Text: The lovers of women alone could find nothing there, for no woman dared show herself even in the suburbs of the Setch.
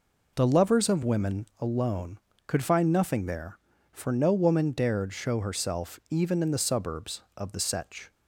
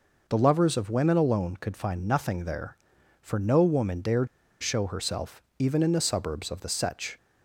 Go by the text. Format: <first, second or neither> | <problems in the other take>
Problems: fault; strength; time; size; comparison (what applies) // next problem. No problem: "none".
first | pauses between "dared" and "show"; slight; at 4.2 s; 0.34 s long // pauses between "herself" and "even"; slight; at 5.4 s; 0.18 s long